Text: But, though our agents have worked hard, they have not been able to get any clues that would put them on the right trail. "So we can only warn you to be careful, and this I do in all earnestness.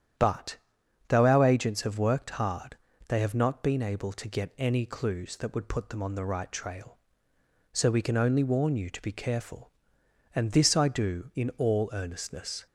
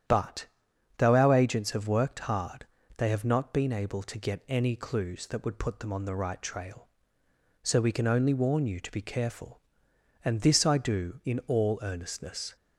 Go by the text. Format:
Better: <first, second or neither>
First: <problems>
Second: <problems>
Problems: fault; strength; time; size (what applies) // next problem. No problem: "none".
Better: neither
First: starts louder than the rest; strong; until 1.7 s; 9.5 dB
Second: starts louder than the rest; strong; until 1.6 s; 9.5 dB